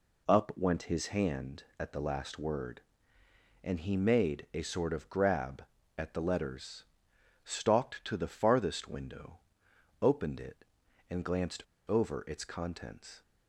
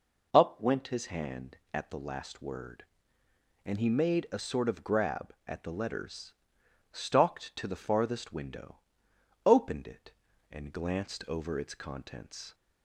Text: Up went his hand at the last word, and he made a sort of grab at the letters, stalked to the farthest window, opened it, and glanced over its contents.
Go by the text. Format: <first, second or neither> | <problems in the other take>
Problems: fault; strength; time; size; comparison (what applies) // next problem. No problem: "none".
second | pauses between "glanced" and "over"; slight; at 11.6 s; 0.28 s long